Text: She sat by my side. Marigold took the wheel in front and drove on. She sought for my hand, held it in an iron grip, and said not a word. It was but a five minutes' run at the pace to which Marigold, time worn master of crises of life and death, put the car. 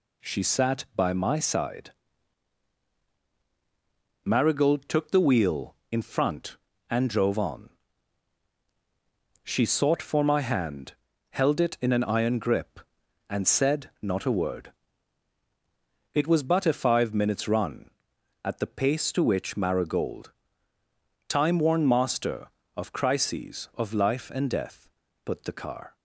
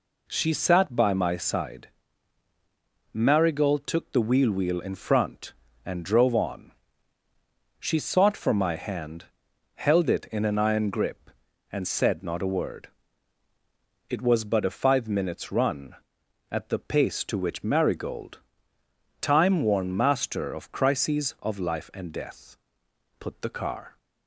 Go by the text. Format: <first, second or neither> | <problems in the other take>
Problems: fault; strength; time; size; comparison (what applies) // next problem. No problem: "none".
first | says "wheel" twice; at 4.5 s